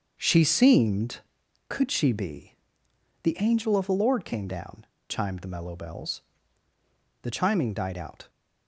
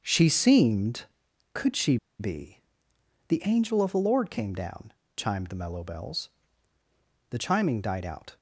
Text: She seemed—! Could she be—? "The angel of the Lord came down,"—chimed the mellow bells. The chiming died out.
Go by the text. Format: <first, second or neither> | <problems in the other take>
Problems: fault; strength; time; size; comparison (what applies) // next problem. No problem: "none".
first | starts louder than the rest; until 1.0 s; 6.5 dB; also in the first // pauses between "she" and "be"; slight; at 1.9 s; 0.22 s long